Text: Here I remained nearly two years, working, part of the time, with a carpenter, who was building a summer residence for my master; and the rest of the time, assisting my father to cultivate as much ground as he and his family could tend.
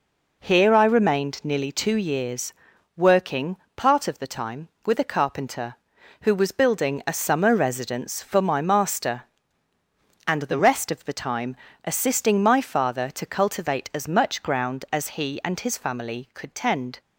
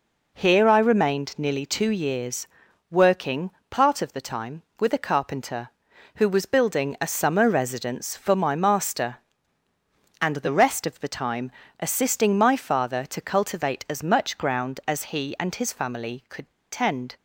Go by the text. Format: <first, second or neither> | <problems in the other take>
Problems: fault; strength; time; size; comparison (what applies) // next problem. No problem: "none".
first | pauses between "could" and "tend"; slight; at 16.5 s; 0.19 s long